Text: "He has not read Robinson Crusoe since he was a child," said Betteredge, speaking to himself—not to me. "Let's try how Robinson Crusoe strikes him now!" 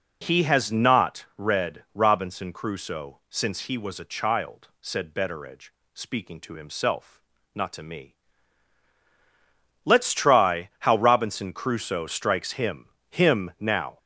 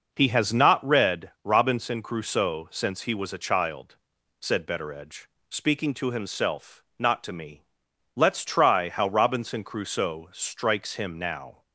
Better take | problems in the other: second | says "him" twice; at 13.0 s

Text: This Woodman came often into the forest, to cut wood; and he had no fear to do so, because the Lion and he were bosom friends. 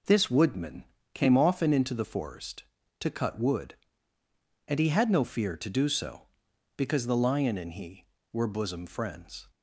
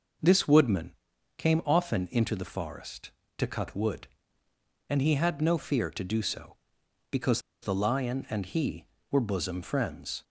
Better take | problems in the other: first | pauses between "Woodman" and "came"; noticeable; at 0.9 s; 0.46 s long; slight in the first // pauses between "because" and "the"; slight; at 7.4 s; 0.21 s long

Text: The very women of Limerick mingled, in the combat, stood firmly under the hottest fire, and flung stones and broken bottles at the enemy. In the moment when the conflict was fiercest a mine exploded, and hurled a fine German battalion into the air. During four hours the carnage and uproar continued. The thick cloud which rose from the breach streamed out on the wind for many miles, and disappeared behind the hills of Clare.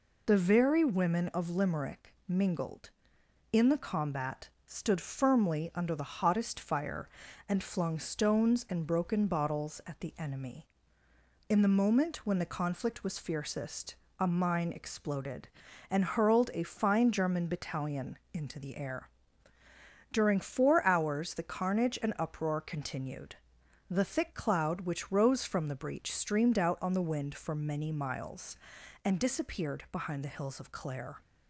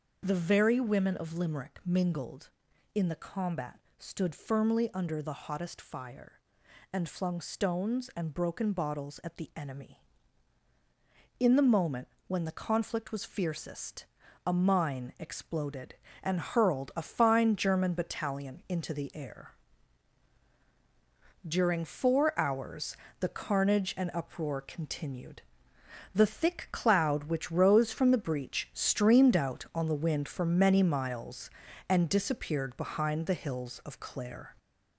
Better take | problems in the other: first | gets louder; noticeable; throughout; 4 dB // starts louder than the rest; noticeable; until 1.2 s; 6 dB // pauses between "moment" and "when"; slight; at 12.0 s; 0.18 s long // pauses between "fiercest" and "a"; at 14.0 s; 0.40 s long; slight in the first // pauses between "hours" and "the"; slight; at 22.9 s; 0.24 s long

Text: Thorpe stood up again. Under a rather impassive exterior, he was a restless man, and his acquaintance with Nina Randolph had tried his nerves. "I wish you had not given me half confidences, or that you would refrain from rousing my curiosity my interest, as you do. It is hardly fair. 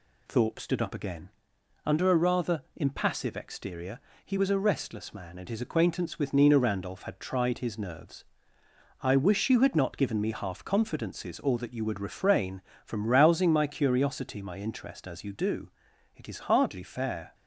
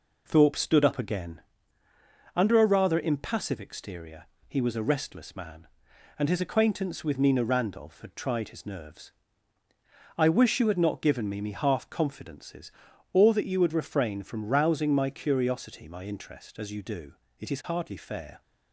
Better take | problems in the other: first | says "me" twice; at 11.4 s

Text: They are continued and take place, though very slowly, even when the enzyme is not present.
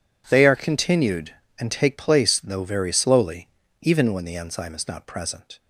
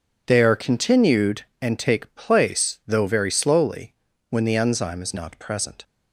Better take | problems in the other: first | skips "even"; at 4.1 s

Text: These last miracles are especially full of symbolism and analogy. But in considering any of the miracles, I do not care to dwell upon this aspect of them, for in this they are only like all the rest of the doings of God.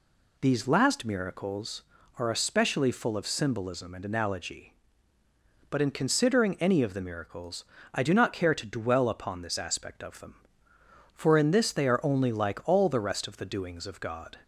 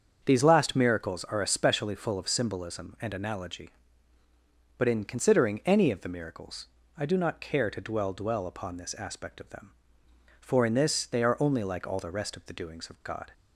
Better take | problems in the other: first | starts louder than the rest; strong; until 1.2 s; 7 dB // says "dwell" twice; at 8.1 s

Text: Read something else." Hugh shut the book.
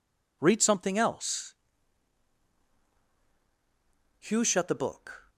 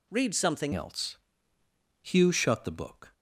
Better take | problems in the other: first | changes voice at "else"; from 0.7 s on; 2.4 s long

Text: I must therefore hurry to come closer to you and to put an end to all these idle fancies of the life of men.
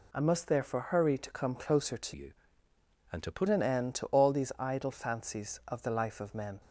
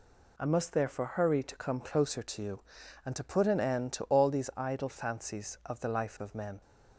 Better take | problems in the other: second | changes voice from "you" to "put"; from 2.1 to 3.4 s; 1.3 s long

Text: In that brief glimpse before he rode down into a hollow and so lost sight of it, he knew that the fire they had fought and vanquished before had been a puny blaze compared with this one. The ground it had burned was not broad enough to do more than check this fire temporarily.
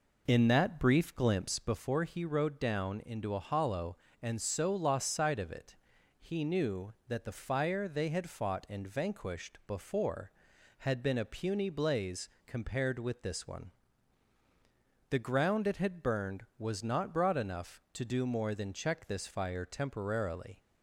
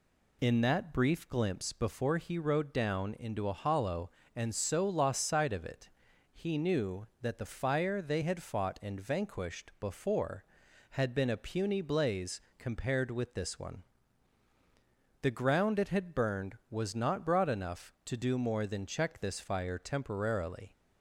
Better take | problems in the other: second | starts louder than the rest; noticeable; until 1.7 s; 4.5 dB // pauses between "blaze" and "compared"; slight; at 12.2 s; 0.16 s long; slight in the second

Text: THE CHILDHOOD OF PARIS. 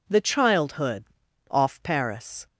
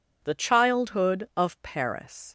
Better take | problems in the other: second | says "Off" for "OF"; at 1.4 s

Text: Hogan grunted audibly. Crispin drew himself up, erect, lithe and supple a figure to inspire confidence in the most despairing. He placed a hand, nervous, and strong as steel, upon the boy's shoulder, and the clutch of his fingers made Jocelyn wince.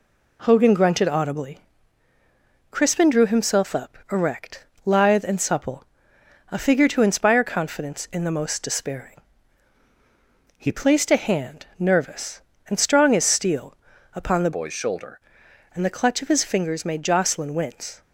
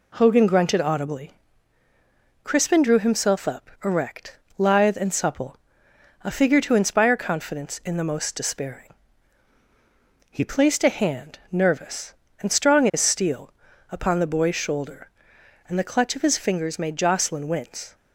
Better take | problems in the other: second | pauses between "supple" and "a"; noticeable; at 5.8 s; 0.66 s long; noticeable in the second // changes voice from "boy's" to "shoulder"; from 14.5 to 15.2 s; 0.7 s long

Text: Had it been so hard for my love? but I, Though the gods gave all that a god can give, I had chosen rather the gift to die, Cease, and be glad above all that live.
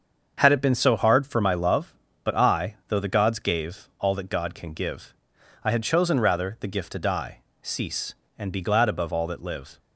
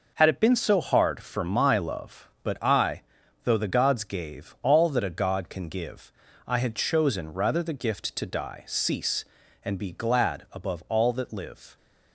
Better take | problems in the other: second | starts louder than the rest; until 1.3 s; 7 dB // skips "a"; at 4.2 s

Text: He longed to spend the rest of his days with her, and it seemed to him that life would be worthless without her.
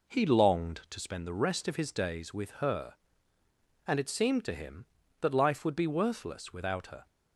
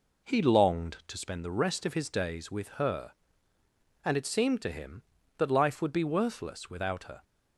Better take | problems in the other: neither | none

